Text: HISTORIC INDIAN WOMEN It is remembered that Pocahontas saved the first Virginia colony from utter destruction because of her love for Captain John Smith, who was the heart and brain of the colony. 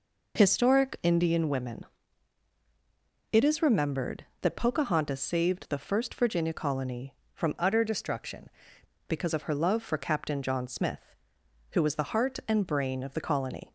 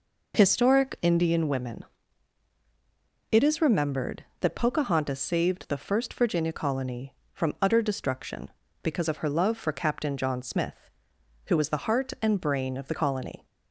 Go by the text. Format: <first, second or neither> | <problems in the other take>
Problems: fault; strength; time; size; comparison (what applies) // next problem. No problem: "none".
second | pauses between "WOMEN" and "It"; strong; at 1.8 s; 1.4 s long; strong in the second // changes voice from "utter" to "destruction"; from 7.5 to 8.4 s; 0.9 s long